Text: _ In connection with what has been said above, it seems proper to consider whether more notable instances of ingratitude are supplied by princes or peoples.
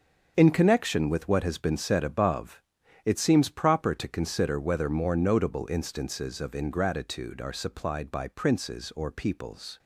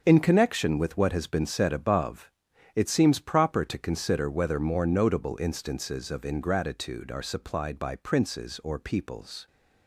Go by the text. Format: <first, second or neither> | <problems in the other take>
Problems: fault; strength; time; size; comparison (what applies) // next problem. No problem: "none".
neither | starts louder than the rest; the same in both